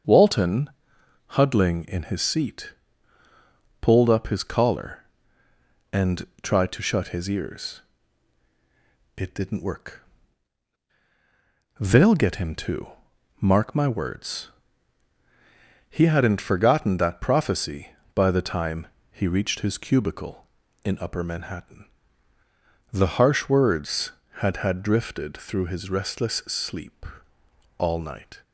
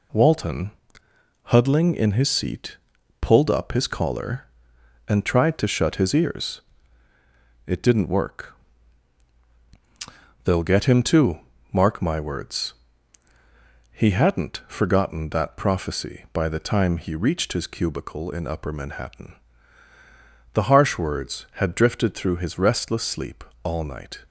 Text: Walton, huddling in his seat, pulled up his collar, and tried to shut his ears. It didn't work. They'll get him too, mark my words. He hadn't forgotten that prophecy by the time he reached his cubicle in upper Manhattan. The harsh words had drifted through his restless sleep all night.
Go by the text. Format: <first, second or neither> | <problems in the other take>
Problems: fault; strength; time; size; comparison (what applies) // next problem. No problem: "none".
second | starts louder than the rest; until 1.6 s; 7 dB // pauses between "and" and "tried"; slight; at 6.2 s; 0.16 s long // pauses between "time" and "he"; slight; at 18.8 s; 0.26 s long // says "had" twice; at 24.5 s // pauses between "sleep" and "all"; noticeable; at 27.0 s; 0.76 s long; slight in the second